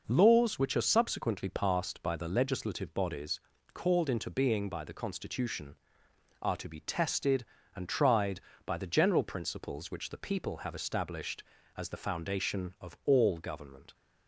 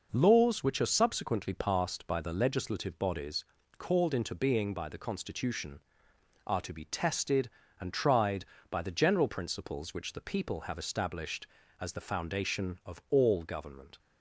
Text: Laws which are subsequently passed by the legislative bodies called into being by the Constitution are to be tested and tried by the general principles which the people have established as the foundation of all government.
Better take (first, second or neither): neither